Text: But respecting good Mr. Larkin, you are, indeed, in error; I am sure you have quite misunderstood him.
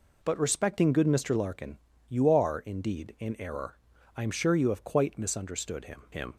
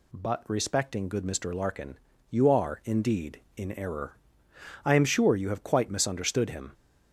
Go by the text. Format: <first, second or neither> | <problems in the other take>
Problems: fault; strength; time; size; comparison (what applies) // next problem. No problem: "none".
second | says "him" twice; at 6.1 s